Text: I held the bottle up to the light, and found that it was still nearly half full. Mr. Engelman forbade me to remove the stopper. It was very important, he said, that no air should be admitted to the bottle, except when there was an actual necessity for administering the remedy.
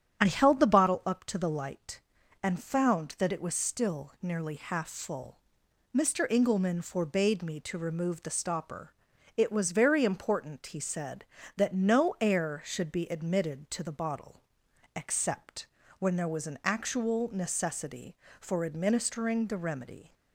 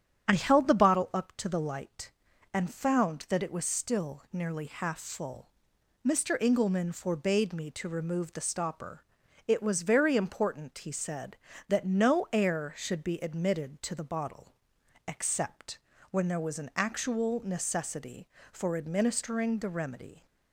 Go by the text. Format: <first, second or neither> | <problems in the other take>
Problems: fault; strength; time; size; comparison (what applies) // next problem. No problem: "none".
neither | starts louder than the rest; strong; the same in both // pauses between "except" and "when"; slight; the same in both